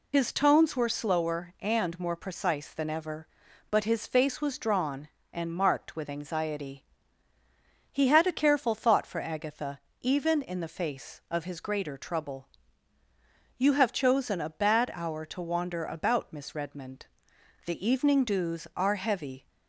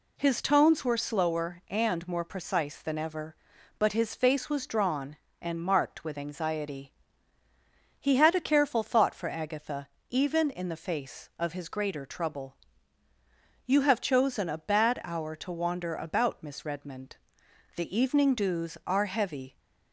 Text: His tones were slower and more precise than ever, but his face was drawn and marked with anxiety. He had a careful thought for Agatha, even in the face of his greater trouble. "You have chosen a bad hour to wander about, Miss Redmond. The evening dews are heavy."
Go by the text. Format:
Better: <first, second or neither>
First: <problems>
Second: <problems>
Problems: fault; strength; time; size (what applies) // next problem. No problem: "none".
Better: second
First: loses the start of "His"; at 0.1 s; 60 ms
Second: none